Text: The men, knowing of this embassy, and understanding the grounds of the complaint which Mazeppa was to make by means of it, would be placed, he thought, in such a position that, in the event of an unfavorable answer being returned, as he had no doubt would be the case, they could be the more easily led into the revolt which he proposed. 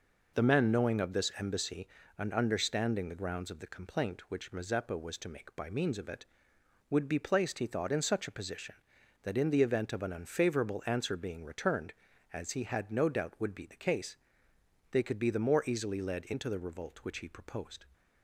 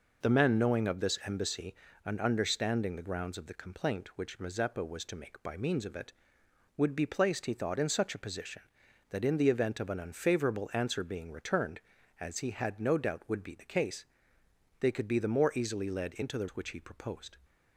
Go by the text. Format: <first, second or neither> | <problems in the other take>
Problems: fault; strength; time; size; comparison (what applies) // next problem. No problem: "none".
first | skips "revolt"; at 16.5 s